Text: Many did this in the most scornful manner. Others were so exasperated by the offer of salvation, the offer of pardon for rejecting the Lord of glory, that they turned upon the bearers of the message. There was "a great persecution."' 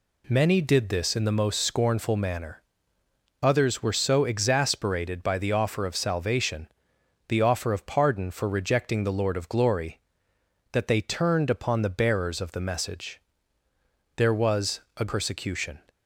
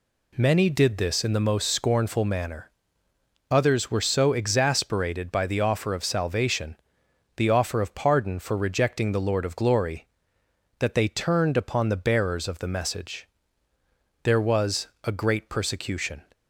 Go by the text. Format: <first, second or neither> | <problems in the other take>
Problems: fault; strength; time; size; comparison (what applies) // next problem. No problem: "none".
second | pauses between "was" and "a"; slight; at 14.7 s; 0.18 s long; slight in the second // skips "great"; at 15.0 s